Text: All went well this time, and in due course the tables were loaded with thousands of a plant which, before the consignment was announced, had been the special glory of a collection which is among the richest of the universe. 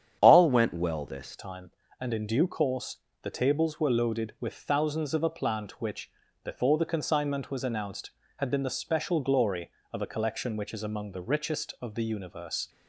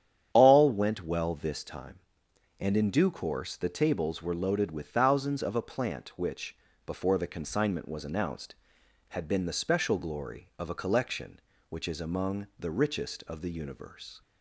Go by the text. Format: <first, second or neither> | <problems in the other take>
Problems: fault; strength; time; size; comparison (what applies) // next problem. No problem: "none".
second | starts louder than the rest; strong; until 1.2 s; 9 dB; strong in the second // changes voice at "time"; from 1.3 s on; 11.3 s long // pauses between "course" and "the"; slight; at 2.9 s; 0.24 s long